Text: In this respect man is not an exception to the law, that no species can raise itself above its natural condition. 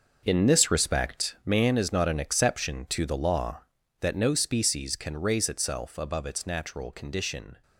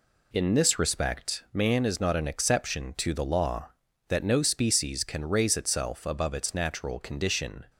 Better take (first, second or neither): second